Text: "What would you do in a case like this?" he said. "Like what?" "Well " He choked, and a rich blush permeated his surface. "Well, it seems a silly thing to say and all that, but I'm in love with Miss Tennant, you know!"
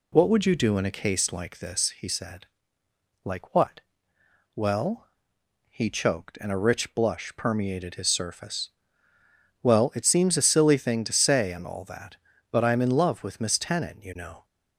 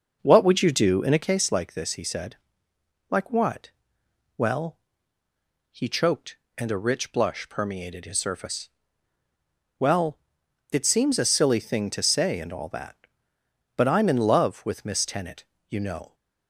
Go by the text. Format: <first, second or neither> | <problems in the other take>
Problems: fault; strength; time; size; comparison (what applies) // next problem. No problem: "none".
first | starts louder than the rest; until 1.3 s; 6.5 dB